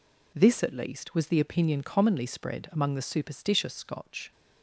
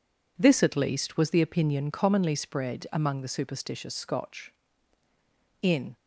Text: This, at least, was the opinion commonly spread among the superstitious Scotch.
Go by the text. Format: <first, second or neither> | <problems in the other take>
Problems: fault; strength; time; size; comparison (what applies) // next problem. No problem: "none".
first | goes on to say "In"; slight; from 5.6 s on; 0.34 s long